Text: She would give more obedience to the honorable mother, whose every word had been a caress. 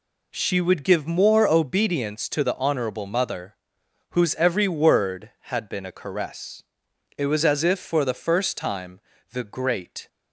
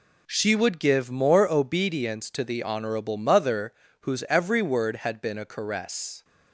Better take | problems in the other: second | goes on to say "It was as if for the first time the great"; strong; from 7.1 s on; 2.9 s long

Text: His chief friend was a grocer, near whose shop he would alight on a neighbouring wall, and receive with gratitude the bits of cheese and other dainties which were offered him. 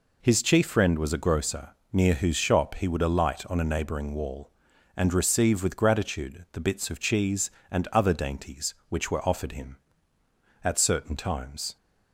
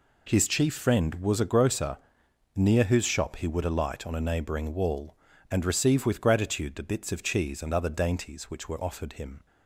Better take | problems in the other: second | goes on to say "At certain times"; noticeable; from 10.6 s on; 1.1 s long

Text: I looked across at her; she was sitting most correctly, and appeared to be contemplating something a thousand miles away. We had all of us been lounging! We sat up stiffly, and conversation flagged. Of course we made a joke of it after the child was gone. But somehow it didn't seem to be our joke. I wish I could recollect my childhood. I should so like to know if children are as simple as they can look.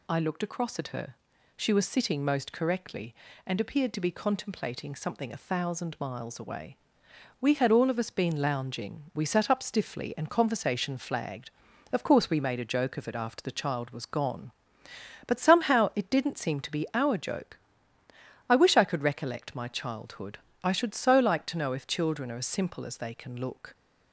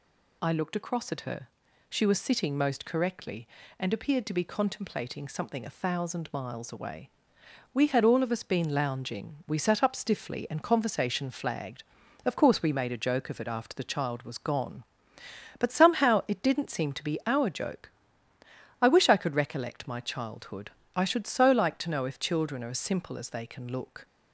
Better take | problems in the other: neither | none

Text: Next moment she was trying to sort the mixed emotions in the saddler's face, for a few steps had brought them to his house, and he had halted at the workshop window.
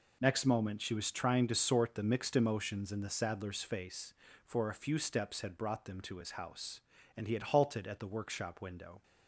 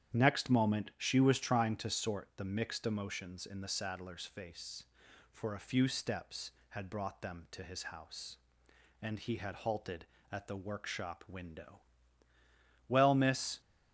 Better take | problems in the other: first | starts louder than the rest; strong; until 1.2 s; 9.5 dB // goes on to say "Well miss"; noticeable; from 12.8 s on; 0.72 s long

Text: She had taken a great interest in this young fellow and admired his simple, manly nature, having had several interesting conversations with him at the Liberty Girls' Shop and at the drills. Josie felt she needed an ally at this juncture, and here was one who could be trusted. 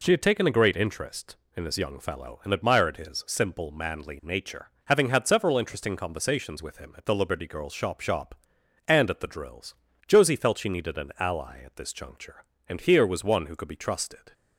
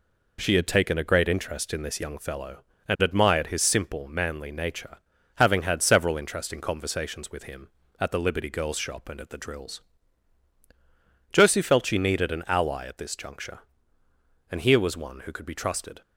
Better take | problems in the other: second | says "Shop" twice; at 8.0 s

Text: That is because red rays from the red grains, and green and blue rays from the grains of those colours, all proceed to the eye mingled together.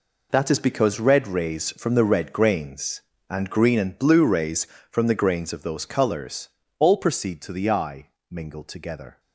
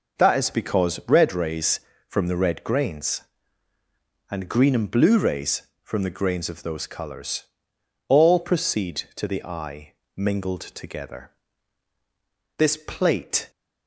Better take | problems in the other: first | pauses between "eye" and "mingled"; at 9.9 s; 0.38 s long; slight in the first // goes on to say "This plate"; noticeable; from 12.5 s on; 0.94 s long

